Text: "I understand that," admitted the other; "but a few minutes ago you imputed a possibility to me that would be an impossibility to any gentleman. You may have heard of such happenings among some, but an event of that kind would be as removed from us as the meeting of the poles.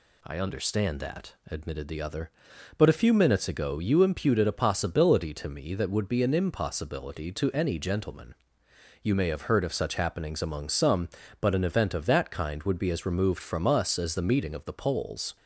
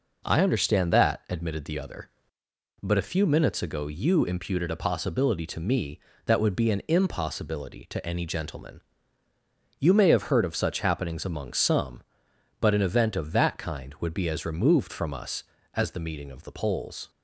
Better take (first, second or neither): neither